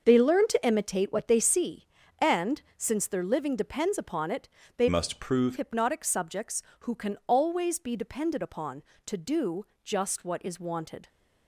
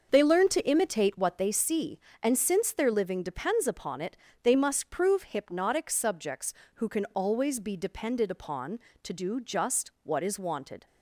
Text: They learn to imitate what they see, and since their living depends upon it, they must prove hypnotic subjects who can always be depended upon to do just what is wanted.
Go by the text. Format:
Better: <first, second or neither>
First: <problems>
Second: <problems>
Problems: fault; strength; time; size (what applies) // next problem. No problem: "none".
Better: second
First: starts louder than the rest; until 1.0 s; 6 dB // pauses between "and" and "since"; slight; at 2.6 s; 0.16 s long // changes voice from "must" to "prove"; from 4.8 to 5.5 s; 0.7 s long // pauses between "do" and "just"; slight; at 9.6 s; 0.20 s long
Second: starts louder than the rest; until 1.1 s; 6.5 dB